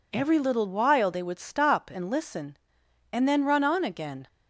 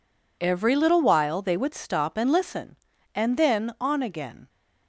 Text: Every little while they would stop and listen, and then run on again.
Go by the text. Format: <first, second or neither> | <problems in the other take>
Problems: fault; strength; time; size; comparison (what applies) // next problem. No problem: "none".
first | skips "run"; at 3.7 s